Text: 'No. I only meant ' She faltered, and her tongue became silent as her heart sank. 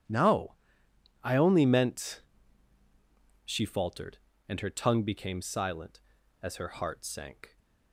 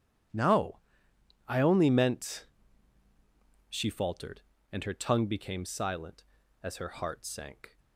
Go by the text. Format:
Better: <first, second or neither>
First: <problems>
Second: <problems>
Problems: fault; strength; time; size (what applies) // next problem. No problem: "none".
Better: neither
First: starts louder than the rest; strong; until 1.7 s; 8.5 dB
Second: starts louder than the rest; strong; until 2.0 s; 8.5 dB